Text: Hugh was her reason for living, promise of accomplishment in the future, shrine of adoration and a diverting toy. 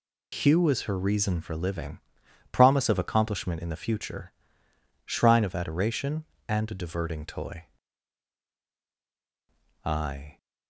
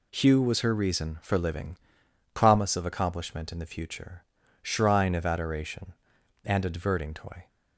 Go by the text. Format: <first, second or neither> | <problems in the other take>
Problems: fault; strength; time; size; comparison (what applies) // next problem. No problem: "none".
second | goes on to say "I"; from 9.8 s on; 0.52 s long